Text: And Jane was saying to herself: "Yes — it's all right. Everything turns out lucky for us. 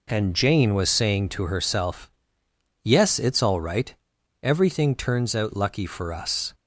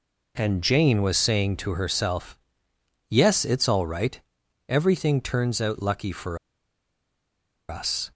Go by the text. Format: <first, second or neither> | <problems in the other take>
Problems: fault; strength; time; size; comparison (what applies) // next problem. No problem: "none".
first | pauses between "for" and "us"; strong; at 6.3 s; 1.3 s long